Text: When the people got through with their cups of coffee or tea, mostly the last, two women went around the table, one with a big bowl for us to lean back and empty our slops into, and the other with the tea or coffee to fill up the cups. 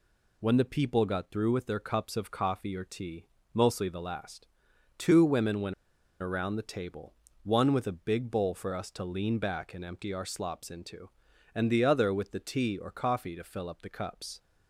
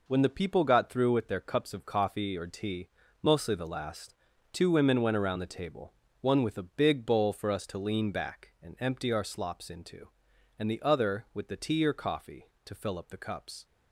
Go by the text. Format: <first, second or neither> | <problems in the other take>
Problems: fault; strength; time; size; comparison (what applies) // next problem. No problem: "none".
second | pauses between "went" and "around"; noticeable; at 5.7 s; 0.47 s long